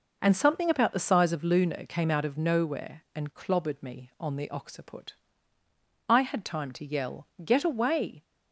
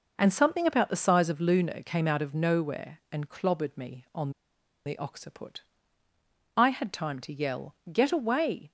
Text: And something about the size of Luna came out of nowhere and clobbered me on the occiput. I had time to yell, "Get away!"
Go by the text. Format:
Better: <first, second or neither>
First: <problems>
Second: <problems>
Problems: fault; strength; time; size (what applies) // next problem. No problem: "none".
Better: first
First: none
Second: pauses between "on" and "the"; noticeable; at 4.2 s; 0.56 s long